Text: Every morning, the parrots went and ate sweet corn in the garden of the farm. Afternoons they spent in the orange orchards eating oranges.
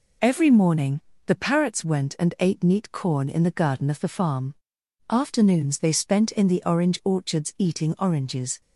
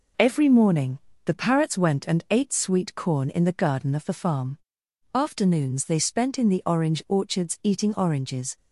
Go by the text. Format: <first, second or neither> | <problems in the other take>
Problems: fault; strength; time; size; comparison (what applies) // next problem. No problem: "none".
second | says "neat" for "sweet"; at 2.6 s